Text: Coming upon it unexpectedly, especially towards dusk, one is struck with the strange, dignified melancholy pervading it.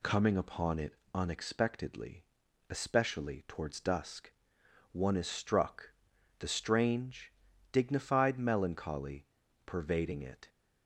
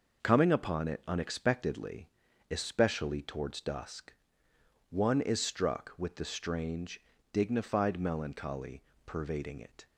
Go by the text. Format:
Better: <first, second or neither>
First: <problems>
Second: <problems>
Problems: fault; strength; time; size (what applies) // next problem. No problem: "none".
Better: second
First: pauses between "it" and "unexpectedly"; slight; at 0.9 s; 0.20 s long // skips "with"; at 6.1 s // pauses between "melancholy" and "pervading"; at 9.2 s; 0.38 s long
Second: pauses between "melancholy" and "pervading"; slight; at 8.8 s; 0.24 s long